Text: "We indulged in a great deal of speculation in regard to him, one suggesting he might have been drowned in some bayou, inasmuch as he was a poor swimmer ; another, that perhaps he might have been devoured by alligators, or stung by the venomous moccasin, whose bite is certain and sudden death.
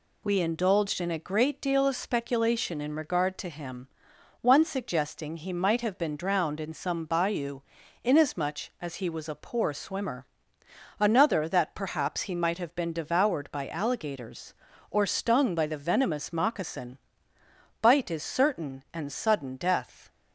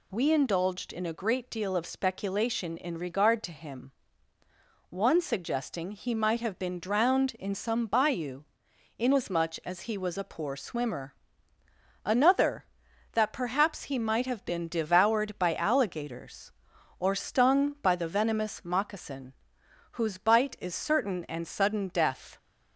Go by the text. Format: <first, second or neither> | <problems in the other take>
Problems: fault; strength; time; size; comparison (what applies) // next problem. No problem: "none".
second | skips "whose"; at 17.3 s